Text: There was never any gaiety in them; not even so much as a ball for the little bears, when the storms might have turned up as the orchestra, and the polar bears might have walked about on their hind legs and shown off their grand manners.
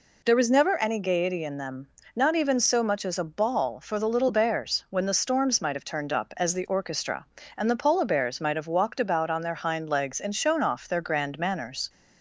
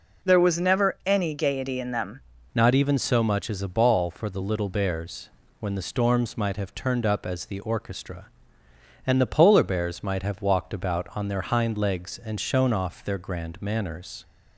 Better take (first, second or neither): first